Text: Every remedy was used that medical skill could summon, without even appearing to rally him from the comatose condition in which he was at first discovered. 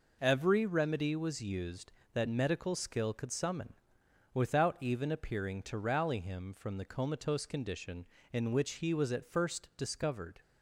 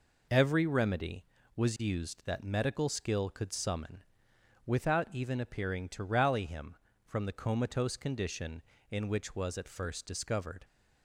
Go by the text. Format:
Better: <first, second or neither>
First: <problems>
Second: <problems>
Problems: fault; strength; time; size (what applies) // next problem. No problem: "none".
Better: first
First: none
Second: skips "he"; at 9.3 s